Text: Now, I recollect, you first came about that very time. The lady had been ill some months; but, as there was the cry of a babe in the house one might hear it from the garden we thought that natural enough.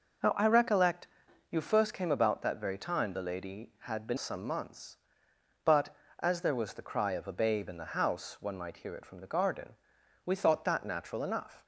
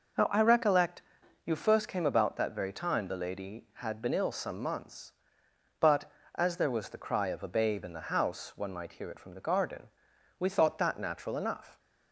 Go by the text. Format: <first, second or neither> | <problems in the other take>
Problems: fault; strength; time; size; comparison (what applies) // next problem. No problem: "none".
second | skips "ill"; at 4.1 s // pauses between "garden" and "we"; noticeable; at 9.7 s; 0.50 s long; noticeable in the second